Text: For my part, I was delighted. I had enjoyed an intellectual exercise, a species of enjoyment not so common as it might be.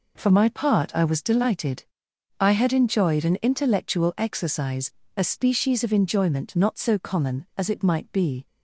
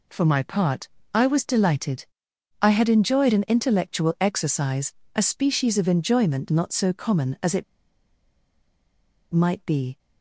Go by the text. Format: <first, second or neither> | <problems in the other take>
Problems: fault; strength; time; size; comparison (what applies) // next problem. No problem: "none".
first | pauses between "it" and "might"; strong; at 7.6 s; 1.7 s long